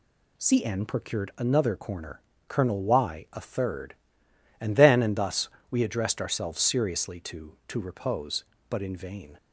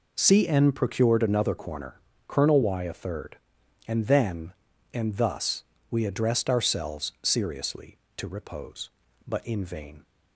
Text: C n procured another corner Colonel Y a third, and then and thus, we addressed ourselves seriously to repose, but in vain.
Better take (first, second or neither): second